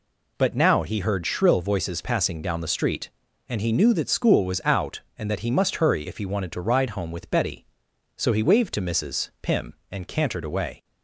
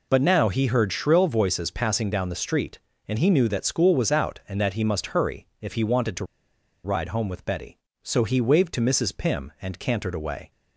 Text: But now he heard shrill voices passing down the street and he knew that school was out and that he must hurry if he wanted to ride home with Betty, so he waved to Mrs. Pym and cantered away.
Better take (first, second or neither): first